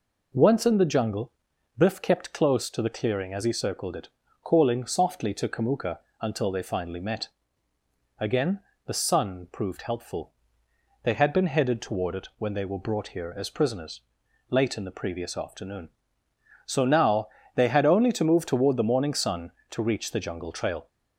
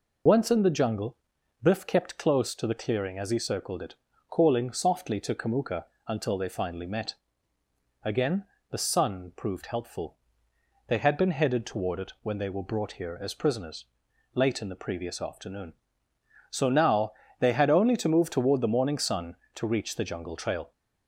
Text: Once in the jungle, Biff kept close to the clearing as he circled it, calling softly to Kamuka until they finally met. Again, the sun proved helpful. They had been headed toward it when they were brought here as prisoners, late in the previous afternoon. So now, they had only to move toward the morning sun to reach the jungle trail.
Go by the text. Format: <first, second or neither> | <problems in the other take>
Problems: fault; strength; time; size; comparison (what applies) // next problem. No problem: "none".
first | loses the start of "Once"; at 0.2 s; 65 ms // pauses between "Kamuka" and "until"; slight; at 5.8 s; 0.24 s long; slight in the first